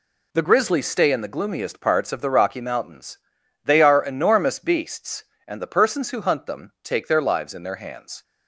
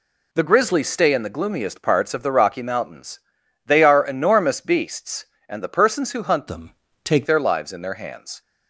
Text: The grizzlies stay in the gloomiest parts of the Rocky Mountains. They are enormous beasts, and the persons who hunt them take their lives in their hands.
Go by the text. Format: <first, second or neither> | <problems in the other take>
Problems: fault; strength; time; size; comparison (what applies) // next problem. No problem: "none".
first | changes voice from "them" to "take"; from 6.4 to 7.2 s; 0.8 s long // pauses between "them" and "take"; slight; at 6.7 s; 0.32 s long